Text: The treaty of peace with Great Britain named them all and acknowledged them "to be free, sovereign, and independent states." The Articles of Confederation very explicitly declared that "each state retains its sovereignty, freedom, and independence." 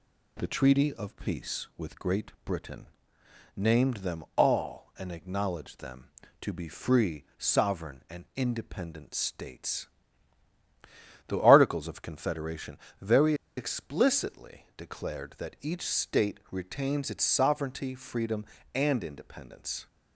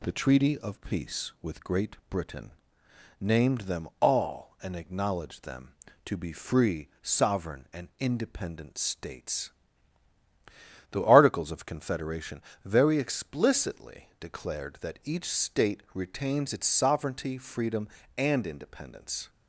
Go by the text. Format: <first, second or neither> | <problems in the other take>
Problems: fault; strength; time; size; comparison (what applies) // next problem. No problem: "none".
second | pauses between "Britain" and "named"; noticeable; at 2.8 s; 0.70 s long; noticeable in the second // pauses between "Confederation" and "very"; slight; at 12.7 s; 0.24 s long; slight in the second // pauses between "very" and "explicitly"; slight; at 13.3 s; 0.23 s long